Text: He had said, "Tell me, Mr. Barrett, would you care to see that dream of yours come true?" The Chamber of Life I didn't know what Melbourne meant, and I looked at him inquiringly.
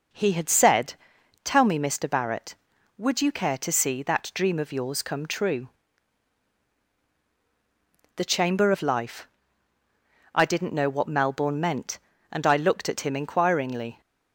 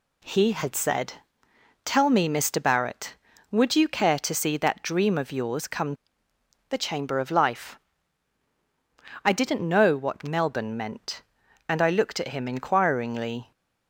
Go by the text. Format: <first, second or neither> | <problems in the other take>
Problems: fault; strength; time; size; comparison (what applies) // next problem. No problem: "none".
first | skips "true"; at 6.3 s // pauses between "Life" and "I"; strong; at 7.7 s; 1.4 s long; also in the first